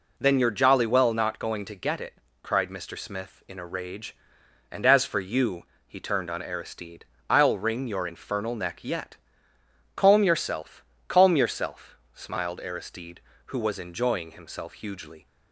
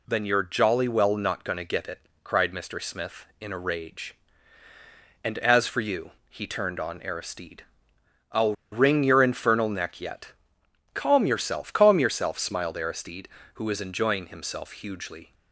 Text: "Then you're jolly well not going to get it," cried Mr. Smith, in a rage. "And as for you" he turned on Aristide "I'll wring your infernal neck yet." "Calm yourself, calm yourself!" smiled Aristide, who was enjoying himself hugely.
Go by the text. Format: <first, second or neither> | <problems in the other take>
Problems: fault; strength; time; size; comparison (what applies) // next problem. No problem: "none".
first | pauses between "you" and "he"; slight; at 6.1 s; 0.18 s long; slight in the first // pauses between "Aristide" and "I'll"; noticeable; at 7.6 s; 0.66 s long; slight in the first // pauses between "I'll" and "wring"; slight; at 8.5 s; 0.19 s long